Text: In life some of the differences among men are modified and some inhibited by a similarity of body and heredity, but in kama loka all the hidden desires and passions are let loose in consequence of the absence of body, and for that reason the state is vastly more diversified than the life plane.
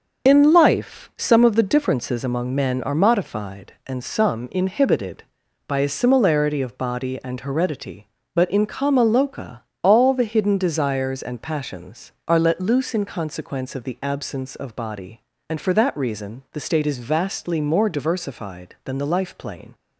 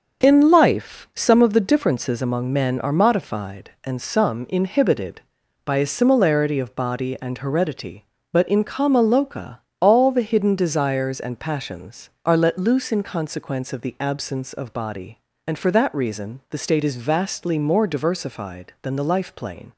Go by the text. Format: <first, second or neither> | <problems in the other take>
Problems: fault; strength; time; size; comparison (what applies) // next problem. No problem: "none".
second | loses the start of "In"; at 0.2 s; 25 ms // starts louder than the rest; until 1.3 s; 6 dB; noticeable in the second // pauses between "loka" and "all"; slight; at 9.6 s; 0.22 s long; slight in the second